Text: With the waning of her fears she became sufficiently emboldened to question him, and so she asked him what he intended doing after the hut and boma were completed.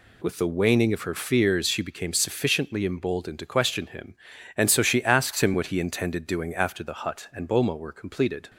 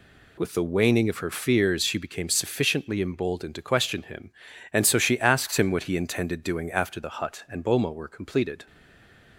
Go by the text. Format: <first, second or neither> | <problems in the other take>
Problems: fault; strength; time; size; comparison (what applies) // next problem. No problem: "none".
first | stays silent after the last word; slight; from 8.6 s on; 0.7 s long